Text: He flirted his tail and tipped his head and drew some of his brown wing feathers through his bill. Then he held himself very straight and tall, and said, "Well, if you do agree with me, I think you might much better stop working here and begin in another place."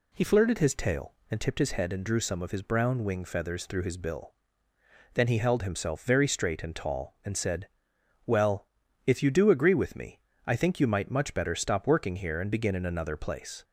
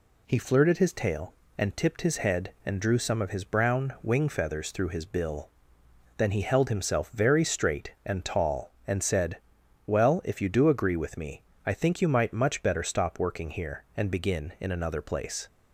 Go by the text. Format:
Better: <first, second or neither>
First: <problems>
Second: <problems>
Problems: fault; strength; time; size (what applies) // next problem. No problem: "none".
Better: neither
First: none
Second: none